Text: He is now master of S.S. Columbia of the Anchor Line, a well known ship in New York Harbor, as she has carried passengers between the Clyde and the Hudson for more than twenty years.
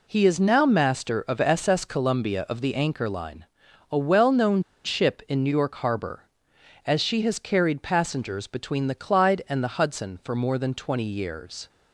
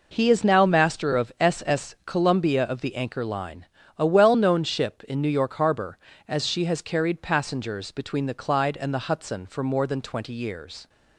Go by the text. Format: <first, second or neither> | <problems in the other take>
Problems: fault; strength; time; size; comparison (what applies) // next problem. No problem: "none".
second | pauses between "known" and "ship"; slight; at 4.6 s; 0.21 s long